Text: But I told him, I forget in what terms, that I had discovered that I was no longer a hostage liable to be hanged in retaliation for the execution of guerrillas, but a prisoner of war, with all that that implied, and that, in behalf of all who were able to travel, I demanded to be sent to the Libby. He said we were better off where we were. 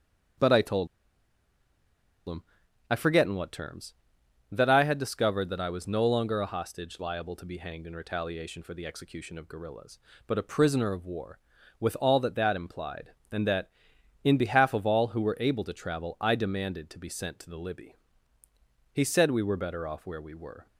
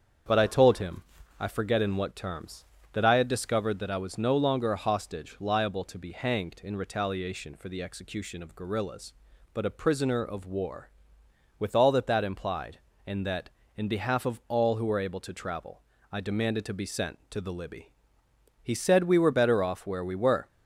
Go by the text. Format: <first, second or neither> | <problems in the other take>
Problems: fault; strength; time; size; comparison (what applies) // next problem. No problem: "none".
second | starts louder than the rest; strong; until 3.2 s; 8.5 dB; strong in the second // pauses between "told" and "him"; strong; at 0.8 s; 1.4 s long